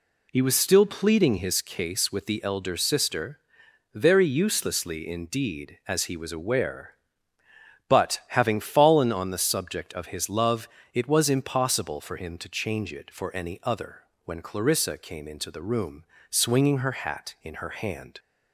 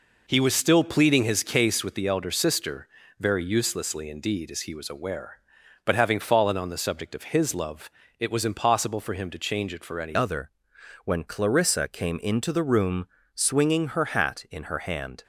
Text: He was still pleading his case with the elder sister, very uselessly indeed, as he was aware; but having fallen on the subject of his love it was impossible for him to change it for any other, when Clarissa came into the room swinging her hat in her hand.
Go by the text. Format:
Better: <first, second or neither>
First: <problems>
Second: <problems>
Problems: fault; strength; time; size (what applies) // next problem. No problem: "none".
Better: first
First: pauses between "love" and "it"; slight; at 10.6 s; 0.26 s long // pauses between "room" and "swinging"; slight; at 16.0 s; 0.24 s long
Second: pauses between "love" and "it"; slight; at 7.8 s; 0.30 s long // changes voice at "other"; from 10.1 s on; 5.1 s long // pauses between "room" and "swinging"; slight; at 13.0 s; 0.26 s long